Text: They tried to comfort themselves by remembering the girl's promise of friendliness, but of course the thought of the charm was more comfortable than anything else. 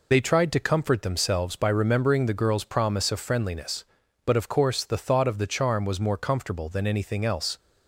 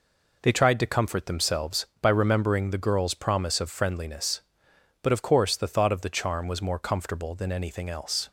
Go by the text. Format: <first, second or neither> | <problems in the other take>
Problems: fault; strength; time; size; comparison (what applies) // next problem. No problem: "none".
second | loses the start of "They"; at 0.1 s; 35 ms